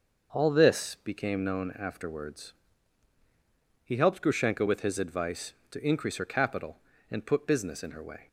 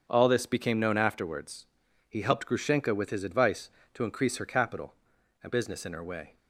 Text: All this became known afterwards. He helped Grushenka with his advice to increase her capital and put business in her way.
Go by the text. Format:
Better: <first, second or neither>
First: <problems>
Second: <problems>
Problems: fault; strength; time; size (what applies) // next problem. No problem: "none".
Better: first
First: starts louder than the rest; until 1.4 s; 6.5 dB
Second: starts louder than the rest; strong; until 1.0 s; 7 dB // skips "put"; at 5.5 s